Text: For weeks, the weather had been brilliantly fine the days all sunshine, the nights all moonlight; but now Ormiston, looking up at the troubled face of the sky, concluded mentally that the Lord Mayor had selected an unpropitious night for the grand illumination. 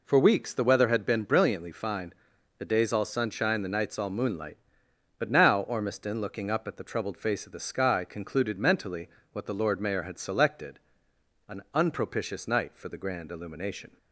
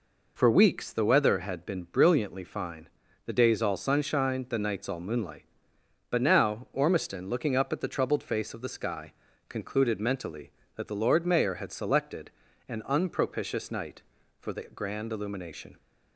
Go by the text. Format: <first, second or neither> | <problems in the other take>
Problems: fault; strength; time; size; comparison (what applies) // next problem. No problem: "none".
second | pauses between "fine" and "the"; at 2.1 s; 0.44 s long; slight in the second // says "what" for "that"; at 9.3 s // pauses between "selected" and "an"; noticeable; at 10.7 s; 0.70 s long; slight in the second